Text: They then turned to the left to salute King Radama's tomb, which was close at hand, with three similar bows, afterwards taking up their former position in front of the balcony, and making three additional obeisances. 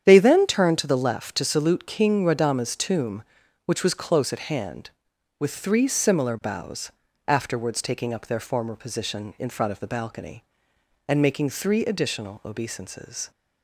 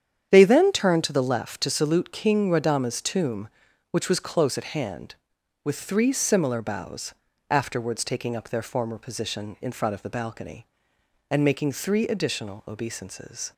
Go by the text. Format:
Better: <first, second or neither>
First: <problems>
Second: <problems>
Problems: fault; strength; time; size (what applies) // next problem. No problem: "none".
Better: neither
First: starts louder than the rest; strong; until 1.0 s; 9 dB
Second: starts louder than the rest; strong; until 1.3 s; 9 dB